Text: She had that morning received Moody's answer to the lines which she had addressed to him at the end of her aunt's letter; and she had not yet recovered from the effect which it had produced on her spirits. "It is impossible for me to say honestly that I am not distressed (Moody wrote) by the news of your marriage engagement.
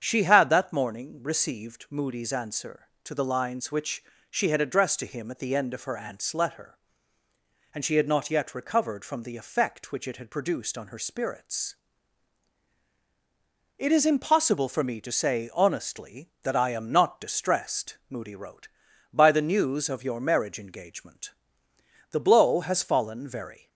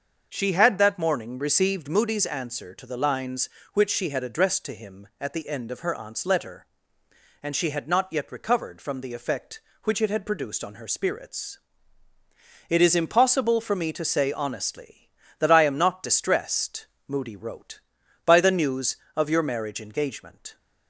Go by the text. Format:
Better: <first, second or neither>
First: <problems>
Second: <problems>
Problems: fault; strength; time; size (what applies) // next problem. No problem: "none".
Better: second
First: starts louder than the rest; strong; until 1.0 s; 8 dB // pauses between "which" and "she"; slight; at 4.0 s; 0.28 s long // goes on to say "The blow has fallen very"; from 22.0 s on; 1.6 s long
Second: starts louder than the rest; until 1.3 s; 6.5 dB